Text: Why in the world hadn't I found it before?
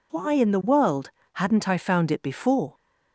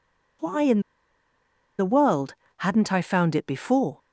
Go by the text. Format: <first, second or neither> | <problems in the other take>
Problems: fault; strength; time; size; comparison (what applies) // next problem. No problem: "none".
first | pauses between "in" and "the"; at 0.7 s; 0.98 s long // pauses between "world" and "hadn't"; slight; at 2.3 s; 0.26 s long; slight in the first